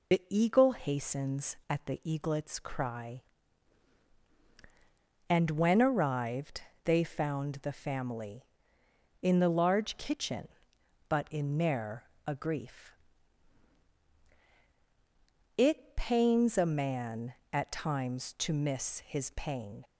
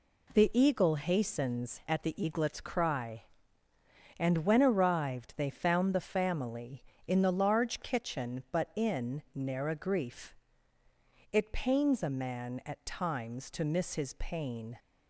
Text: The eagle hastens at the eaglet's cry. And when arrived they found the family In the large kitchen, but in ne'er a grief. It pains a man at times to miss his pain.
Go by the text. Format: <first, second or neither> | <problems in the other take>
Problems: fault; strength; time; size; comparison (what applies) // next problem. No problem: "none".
second | loses the start of "The"; at 0.1 s; 55 ms // pauses between "arrived" and "they"; slight; at 6.6 s; 0.24 s long // pauses between "ne'er" and "a"; slight; at 12.0 s; 0.22 s long